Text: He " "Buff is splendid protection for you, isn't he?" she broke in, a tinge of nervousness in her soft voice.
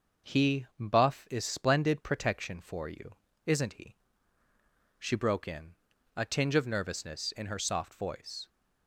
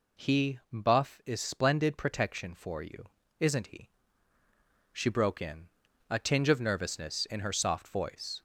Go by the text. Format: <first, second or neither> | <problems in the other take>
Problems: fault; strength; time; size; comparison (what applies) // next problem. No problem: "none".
first | gets louder; throughout; 3.5 dB